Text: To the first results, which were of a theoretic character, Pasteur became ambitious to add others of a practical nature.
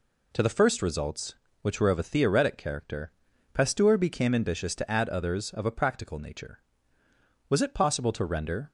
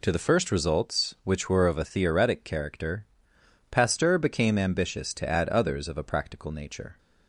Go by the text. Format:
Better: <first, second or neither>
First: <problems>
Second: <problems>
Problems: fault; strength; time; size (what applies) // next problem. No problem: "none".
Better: second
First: goes on to say "Was it possible to render"; noticeable; from 7.4 s on; 1.2 s long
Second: none